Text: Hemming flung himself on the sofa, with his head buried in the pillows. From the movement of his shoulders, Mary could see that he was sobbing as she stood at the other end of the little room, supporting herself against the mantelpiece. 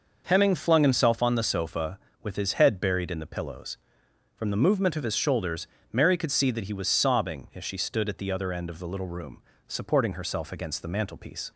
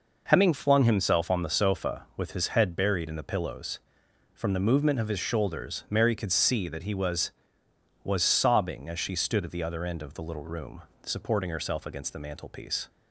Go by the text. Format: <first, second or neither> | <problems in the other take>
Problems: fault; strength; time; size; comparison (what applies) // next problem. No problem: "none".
first | says "was" twice; at 8.0 s